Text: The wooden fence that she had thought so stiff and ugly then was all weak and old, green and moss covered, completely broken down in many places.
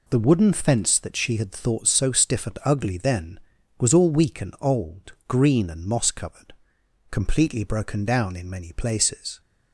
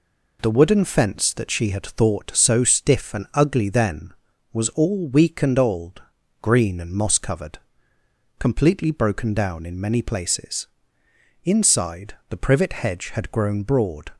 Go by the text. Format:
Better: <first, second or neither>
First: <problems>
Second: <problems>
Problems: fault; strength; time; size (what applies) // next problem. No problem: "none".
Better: first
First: none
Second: goes on to say "Inside the privet hedge had grown broad"; strong; from 11.4 s on; 2.6 s long